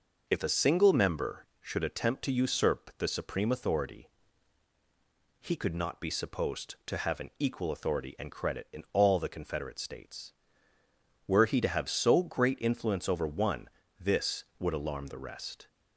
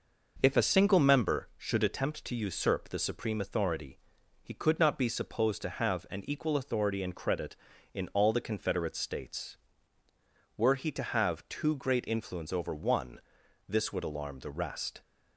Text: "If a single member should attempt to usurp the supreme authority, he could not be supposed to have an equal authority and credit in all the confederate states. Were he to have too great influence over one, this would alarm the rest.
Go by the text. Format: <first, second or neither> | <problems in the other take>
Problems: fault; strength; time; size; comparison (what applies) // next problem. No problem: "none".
second | says "so" for "too"; at 11.8 s